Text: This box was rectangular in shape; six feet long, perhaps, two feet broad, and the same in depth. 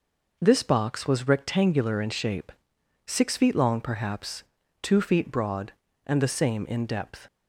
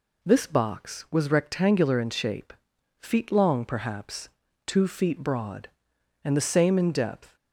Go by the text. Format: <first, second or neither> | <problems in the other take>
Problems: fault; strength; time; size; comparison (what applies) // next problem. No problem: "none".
first | skips "six"; at 2.7 s